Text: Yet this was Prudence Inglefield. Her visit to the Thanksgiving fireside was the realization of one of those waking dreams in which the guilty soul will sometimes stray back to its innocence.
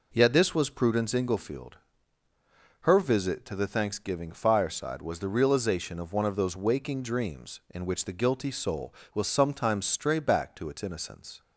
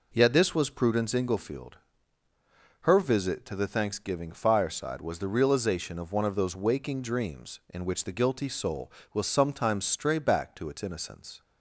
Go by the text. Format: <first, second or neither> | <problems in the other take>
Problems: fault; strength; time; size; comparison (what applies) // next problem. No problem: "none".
neither | none